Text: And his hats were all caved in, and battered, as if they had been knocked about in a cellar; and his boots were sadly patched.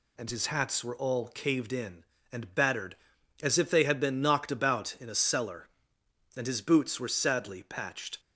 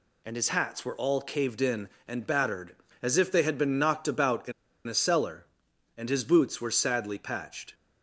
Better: first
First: none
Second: pauses between "in" and "a"; at 4.5 s; 0.37 s long

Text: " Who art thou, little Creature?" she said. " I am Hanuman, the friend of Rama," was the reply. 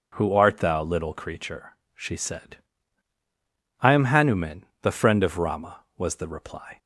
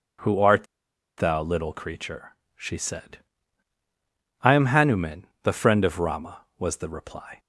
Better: first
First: none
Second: pauses between "art" and "thou"; noticeable; at 0.6 s; 0.52 s long

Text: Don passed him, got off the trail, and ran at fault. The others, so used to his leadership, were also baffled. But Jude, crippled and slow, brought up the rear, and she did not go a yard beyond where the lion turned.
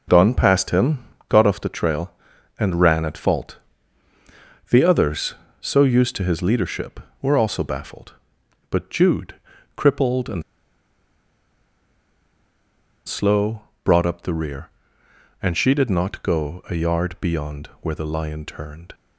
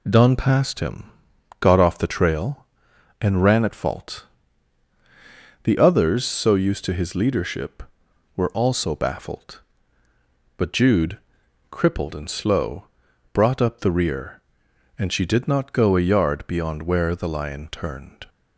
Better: second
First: pauses between "and" and "slow"; strong; at 10.4 s; 2.6 s long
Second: none

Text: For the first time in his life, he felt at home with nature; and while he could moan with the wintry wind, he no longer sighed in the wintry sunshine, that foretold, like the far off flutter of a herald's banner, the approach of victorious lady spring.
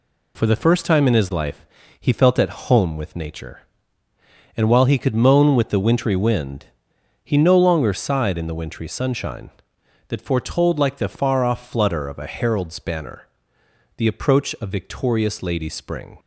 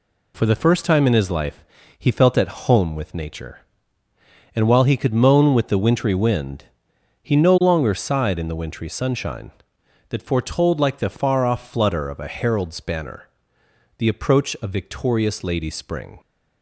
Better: neither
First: none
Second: none

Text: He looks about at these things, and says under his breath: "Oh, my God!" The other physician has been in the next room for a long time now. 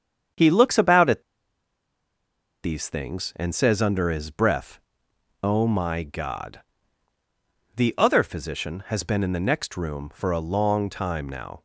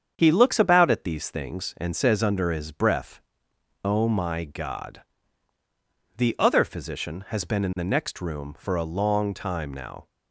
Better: second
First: starts louder than the rest; strong; until 2.7 s; 7.5 dB // pauses between "at" and "these"; strong; at 1.2 s; 1.4 s long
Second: starts louder than the rest; strong; until 1.1 s; 7.5 dB

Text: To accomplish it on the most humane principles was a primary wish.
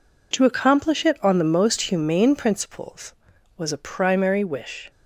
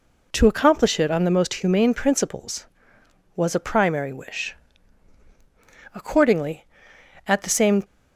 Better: first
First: none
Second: goes on to say "Accordingly at the same"; strong; from 5.9 s on; 1.9 s long

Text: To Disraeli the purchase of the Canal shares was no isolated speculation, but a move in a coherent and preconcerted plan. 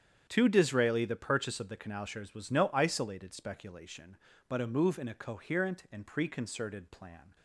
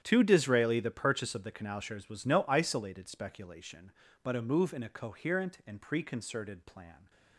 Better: first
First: starts louder than the rest; strong; until 1.2 s; 8.5 dB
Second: gets quieter; strong; throughout; 17 dB // starts louder than the rest; strong; until 1.0 s; 10 dB

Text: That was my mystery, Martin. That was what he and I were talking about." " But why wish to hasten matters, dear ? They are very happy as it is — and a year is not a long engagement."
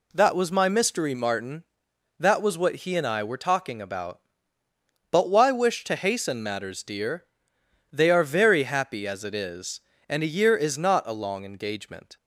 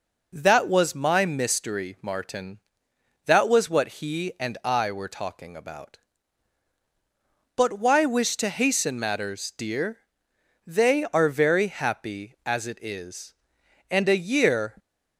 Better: first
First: none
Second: starts louder than the rest; until 1.3 s; 6 dB // stops before "is not a long engagement"; at 14.7 s

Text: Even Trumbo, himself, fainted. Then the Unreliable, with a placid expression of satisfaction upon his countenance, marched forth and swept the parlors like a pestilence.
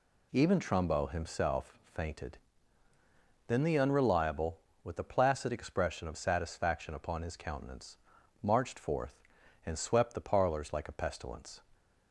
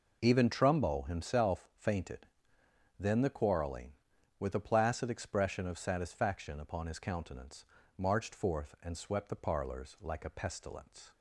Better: first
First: none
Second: says "Quarreling" for "Unreliable"; at 3.2 s

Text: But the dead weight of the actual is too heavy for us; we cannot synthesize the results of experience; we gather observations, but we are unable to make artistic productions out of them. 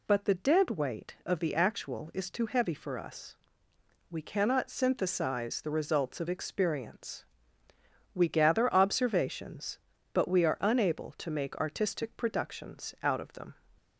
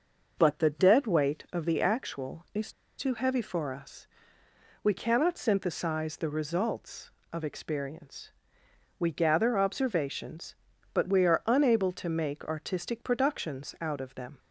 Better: first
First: none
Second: pauses between "is" and "too"; slight; at 2.7 s; 0.28 s long

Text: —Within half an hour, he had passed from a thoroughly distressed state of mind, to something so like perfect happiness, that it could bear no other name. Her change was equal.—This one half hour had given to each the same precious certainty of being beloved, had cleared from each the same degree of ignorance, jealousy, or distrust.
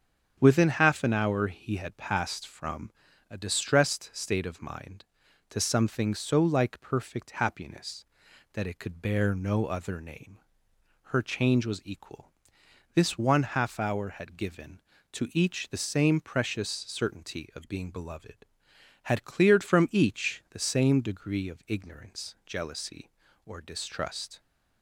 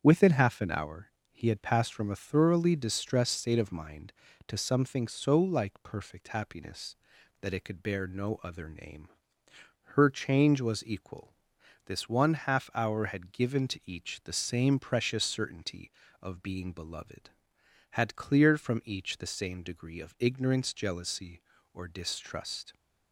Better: second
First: starts louder than the rest; until 1.4 s; 7 dB // pauses between "from" and "a"; slight; at 2.9 s; 0.36 s long // skips "thoroughly"; at 3.3 s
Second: starts louder than the rest; strong; until 1.0 s; 8 dB

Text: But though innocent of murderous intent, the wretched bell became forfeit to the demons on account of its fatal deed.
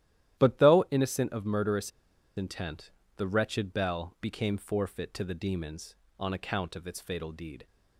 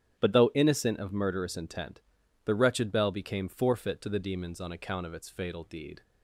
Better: second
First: starts louder than the rest; strong; until 1.4 s; 12.5 dB // pauses between "murderous" and "intent"; noticeable; at 1.9 s; 0.46 s long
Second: starts louder than the rest; strong; until 1.2 s; 11 dB

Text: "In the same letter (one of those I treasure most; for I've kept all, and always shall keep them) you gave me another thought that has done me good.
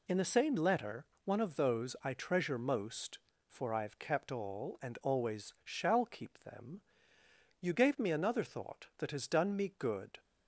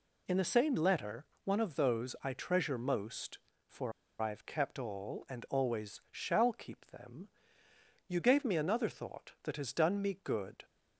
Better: first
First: none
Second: pauses between "for" and "I've"; slight; at 3.9 s; 0.27 s long

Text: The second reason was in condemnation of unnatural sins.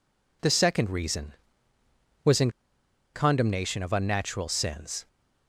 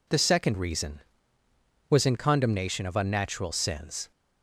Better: second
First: pauses between "in" and "condemnation"; noticeable; at 2.4 s; 0.64 s long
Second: none

